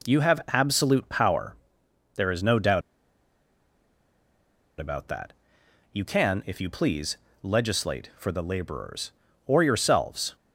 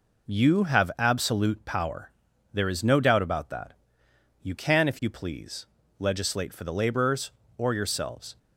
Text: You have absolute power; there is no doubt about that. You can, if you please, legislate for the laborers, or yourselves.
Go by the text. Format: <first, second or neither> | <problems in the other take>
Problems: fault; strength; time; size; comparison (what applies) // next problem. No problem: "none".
second | pauses between "doubt" and "about"; strong; at 2.8 s; 1.9 s long